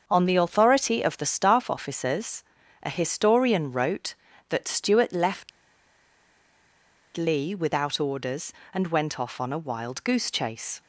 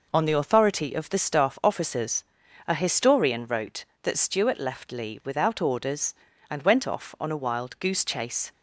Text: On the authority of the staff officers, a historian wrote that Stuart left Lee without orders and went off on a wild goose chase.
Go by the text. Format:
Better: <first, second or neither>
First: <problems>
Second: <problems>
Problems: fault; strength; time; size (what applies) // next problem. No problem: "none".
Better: second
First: starts louder than the rest; until 1.0 s; 6.5 dB // pauses between "left" and "Lee"; strong; at 5.5 s; 1.6 s long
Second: none